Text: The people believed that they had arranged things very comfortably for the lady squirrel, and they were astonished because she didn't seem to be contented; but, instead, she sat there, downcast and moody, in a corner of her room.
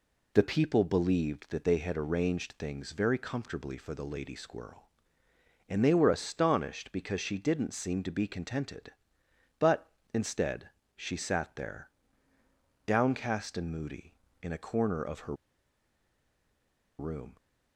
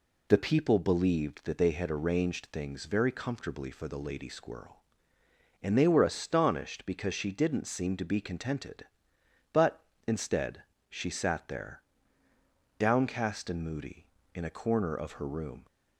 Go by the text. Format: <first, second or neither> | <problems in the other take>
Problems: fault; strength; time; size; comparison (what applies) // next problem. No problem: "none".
second | pauses between "her" and "room"; strong; at 15.3 s; 1.6 s long